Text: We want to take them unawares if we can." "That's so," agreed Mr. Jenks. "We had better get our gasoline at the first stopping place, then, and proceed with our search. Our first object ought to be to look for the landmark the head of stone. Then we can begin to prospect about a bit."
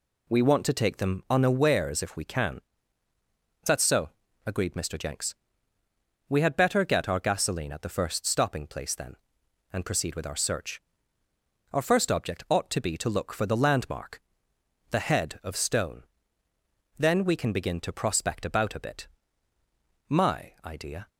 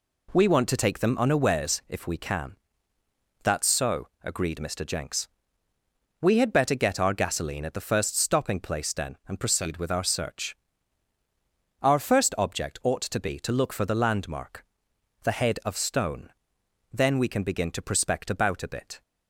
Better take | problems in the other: second | pauses between "landmark" and "the"; noticeable; at 14.2 s; 0.68 s long; noticeable in the second // goes on to say "My idea"; noticeable; from 20.0 s on; 1.0 s long

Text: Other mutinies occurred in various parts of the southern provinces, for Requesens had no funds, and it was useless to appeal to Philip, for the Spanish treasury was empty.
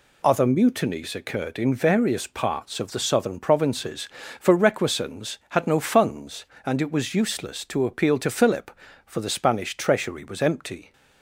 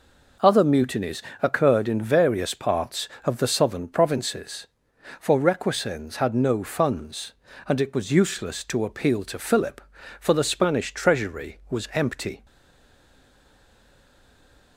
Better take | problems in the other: first | pauses between "mutinies" and "occurred"; slight; at 1.2 s; 0.20 s long // stays silent after the last word; from 12.4 s on; 2.3 s long

